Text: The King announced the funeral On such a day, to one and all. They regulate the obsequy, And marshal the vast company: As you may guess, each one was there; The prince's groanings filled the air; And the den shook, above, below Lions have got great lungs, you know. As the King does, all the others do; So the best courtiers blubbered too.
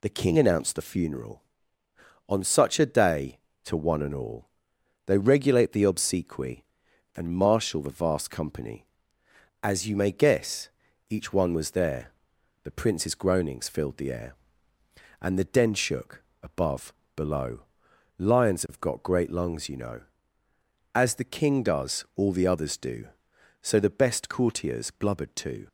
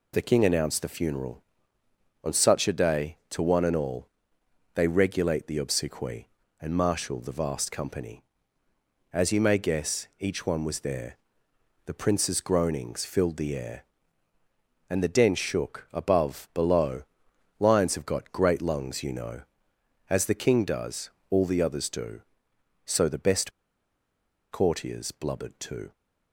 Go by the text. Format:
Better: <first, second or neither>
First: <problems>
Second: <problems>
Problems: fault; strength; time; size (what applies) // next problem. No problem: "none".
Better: first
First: pauses between "below" and "Lions"; noticeable; at 17.6 s; 0.56 s long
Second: pauses between "below" and "Lions"; noticeable; at 17.0 s; 0.56 s long // pauses between "best" and "courtiers"; at 23.5 s; 1.0 s long